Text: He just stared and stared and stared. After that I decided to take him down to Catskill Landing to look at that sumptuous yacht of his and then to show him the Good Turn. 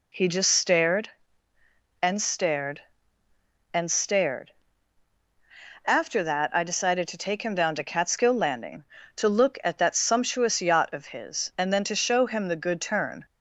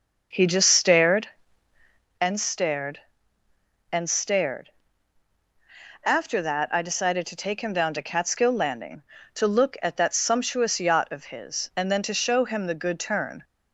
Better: first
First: none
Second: starts louder than the rest; noticeable; until 2.2 s; 6 dB

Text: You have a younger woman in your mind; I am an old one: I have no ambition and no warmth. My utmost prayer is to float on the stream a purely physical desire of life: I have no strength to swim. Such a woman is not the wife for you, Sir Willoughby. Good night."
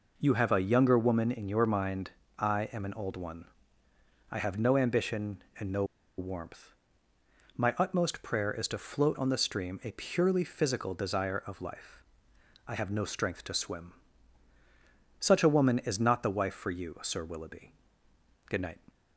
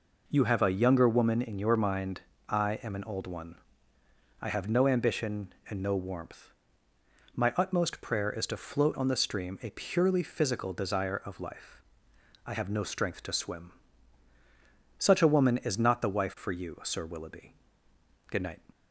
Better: second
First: pauses between "no" and "warmth"; slight; at 5.8 s; 0.34 s long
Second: none

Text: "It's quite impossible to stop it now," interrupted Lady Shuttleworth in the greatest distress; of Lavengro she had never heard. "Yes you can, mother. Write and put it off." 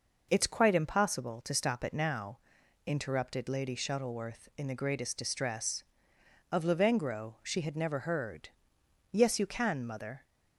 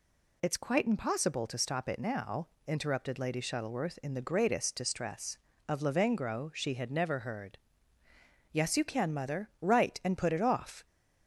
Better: second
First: stops before "Write and put it off"; at 10.2 s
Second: none

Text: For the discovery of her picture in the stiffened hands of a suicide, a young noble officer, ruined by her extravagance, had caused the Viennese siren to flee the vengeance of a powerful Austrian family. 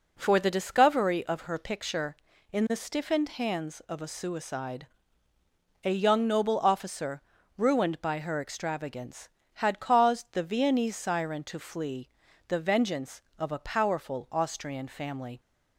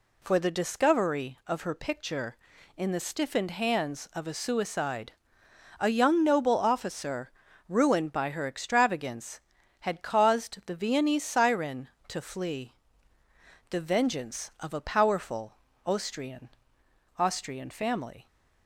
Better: first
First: pauses between "flee" and "the"; at 12.1 s; 0.38 s long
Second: pauses between "flee" and "the"; noticeable; at 12.7 s; 0.98 s long // pauses between "powerful" and "Austrian"; slight; at 15.5 s; 0.28 s long // says "Austrian" twice; at 17.1 s

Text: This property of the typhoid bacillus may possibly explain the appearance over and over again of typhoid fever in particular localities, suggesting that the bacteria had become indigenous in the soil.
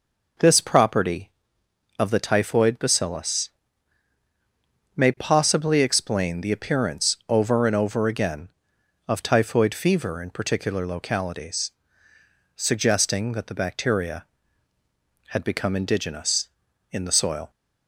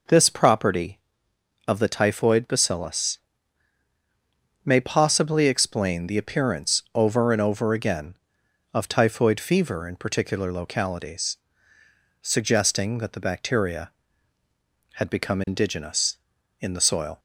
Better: neither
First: pauses between "bacillus" and "may"; strong; at 3.4 s; 1.4 s long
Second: pauses between "bacillus" and "may"; strong; at 3.1 s; 1.4 s long

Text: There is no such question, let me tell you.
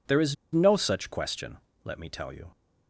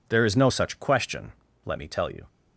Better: second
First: pauses between "is" and "no"; slight; at 0.3 s; 0.17 s long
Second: none

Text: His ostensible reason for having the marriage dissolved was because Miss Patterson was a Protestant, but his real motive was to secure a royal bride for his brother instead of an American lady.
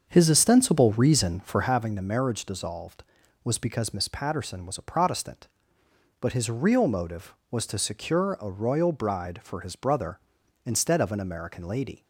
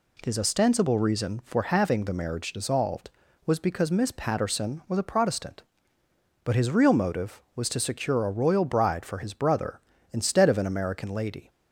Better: second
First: starts louder than the rest; until 1.8 s; 7 dB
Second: none

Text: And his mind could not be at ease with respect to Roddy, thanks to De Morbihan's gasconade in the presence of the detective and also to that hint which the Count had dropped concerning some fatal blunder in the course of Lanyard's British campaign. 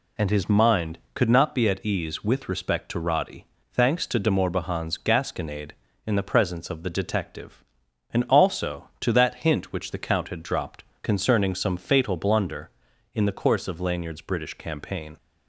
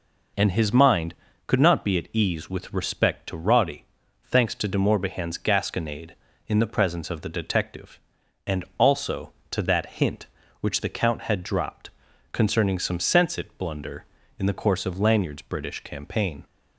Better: first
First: pauses between "dropped" and "concerning"; slight; at 10.8 s; 0.18 s long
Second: pauses between "dropped" and "concerning"; at 11.8 s; 0.44 s long // says "sensit" for "fatal"; at 12.9 s

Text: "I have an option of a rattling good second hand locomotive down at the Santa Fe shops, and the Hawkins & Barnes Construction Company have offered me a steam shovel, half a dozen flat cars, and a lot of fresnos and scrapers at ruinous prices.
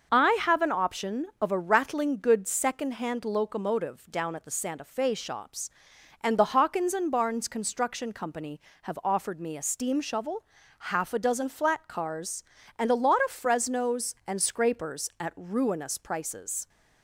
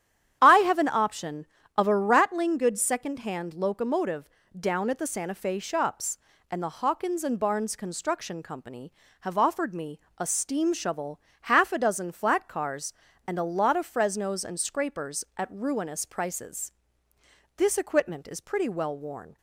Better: first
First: none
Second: starts louder than the rest; strong; until 1.4 s; 10 dB // pauses between "locomotive" and "down"; slight; at 4.2 s; 0.30 s long // pauses between "me" and "a"; slight; at 9.9 s; 0.20 s long // goes on to say "This equipment is pretty well worn"; strong; from 17.5 s on; 1.8 s long

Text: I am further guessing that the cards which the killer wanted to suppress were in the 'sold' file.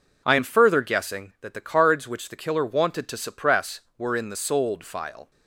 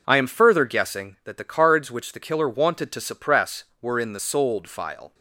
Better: neither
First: none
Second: none

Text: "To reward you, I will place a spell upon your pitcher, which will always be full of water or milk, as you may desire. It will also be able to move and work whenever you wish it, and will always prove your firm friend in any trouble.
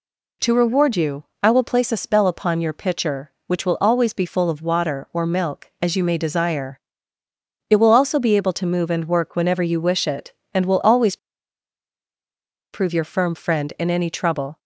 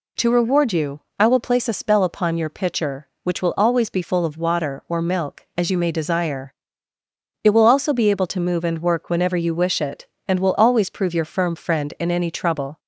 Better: second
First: pauses between "always" and "prove"; strong; at 11.1 s; 1.5 s long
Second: none

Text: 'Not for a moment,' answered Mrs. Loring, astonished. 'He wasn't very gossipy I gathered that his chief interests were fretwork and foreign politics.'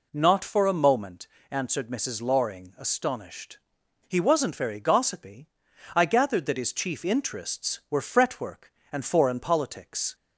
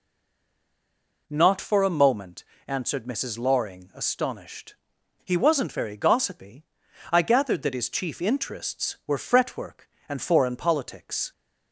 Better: first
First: pauses between "gossipy" and "I"; noticeable; at 5.4 s; 0.46 s long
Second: stays silent before the first word; noticeable; until 1.2 s; 1.2 s long // pauses between "gossipy" and "I"; noticeable; at 6.6 s; 0.46 s long

